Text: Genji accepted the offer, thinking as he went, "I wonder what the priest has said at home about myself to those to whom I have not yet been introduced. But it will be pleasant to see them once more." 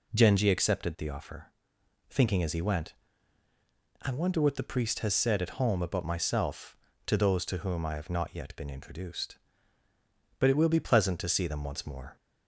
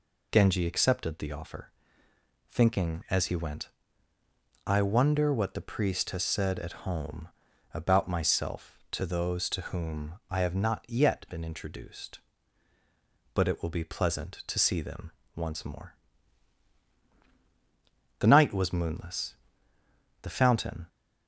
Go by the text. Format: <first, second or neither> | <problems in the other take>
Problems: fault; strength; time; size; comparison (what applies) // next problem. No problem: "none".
first | pauses between "home" and "about"; at 7.2 s; 0.44 s long // pauses between "them" and "once"; slight; at 15.1 s; 0.23 s long // goes on to say "The night was moonless The fountain"; strong; from 18.1 s on; 2.6 s long